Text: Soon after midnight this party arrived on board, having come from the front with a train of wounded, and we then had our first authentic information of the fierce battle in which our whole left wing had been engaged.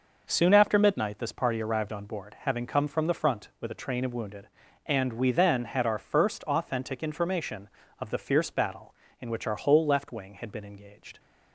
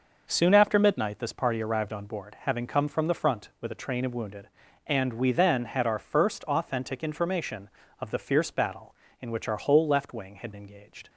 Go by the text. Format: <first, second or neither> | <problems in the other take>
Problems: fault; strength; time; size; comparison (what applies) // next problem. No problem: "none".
first | skips "been"; at 10.5 s